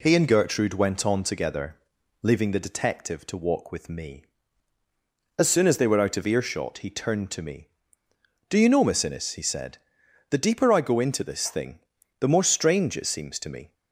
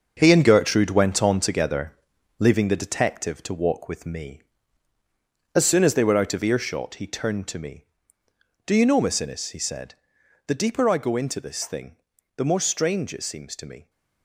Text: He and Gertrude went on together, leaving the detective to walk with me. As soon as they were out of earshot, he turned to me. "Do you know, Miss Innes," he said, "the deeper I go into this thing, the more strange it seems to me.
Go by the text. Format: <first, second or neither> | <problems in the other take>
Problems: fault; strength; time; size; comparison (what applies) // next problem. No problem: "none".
first | gets quieter; strong; throughout; 9 dB